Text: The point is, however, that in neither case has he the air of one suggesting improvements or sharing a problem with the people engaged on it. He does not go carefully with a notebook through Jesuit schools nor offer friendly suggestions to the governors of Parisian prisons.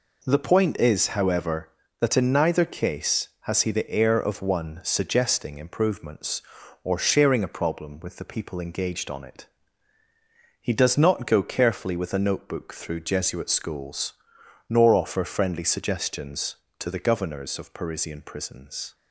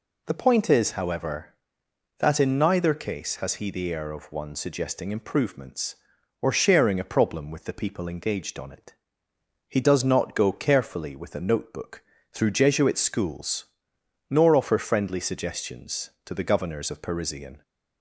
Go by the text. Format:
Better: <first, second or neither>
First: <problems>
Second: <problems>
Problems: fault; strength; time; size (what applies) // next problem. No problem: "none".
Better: first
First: pauses between "schools" and "nor"; noticeable; at 14.1 s; 0.56 s long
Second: pauses between "notebook" and "through"; slight; at 12.0 s; 0.28 s long // pauses between "schools" and "nor"; noticeable; at 13.6 s; 0.64 s long // stops before "prisons"; at 17.6 s